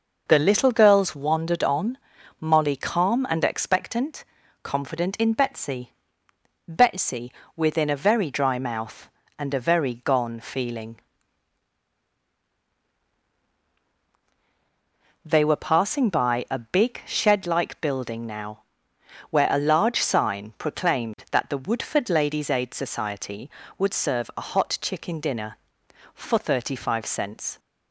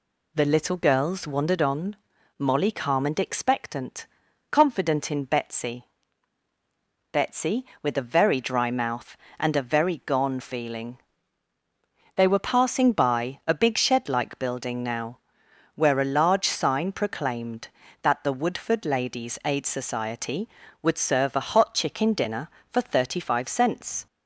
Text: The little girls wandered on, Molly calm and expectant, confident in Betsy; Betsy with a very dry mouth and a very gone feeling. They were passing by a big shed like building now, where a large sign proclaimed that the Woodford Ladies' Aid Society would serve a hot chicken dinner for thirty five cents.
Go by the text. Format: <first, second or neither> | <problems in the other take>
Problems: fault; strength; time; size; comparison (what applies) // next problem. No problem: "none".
second | says "within" for "with"; at 7.5 s